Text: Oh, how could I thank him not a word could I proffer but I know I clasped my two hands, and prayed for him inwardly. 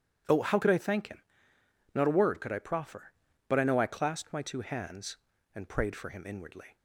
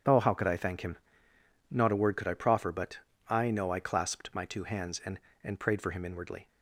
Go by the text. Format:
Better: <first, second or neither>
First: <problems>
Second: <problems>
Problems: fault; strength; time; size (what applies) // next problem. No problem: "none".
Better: first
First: pauses between "him" and "not"; noticeable; at 1.2 s; 0.72 s long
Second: starts louder than the rest; strong; until 1.8 s; 9 dB // pauses between "him" and "not"; noticeable; at 0.9 s; 0.74 s long // pauses between "but" and "I"; slight; at 2.9 s; 0.30 s long // says "and" twice; at 5.4 s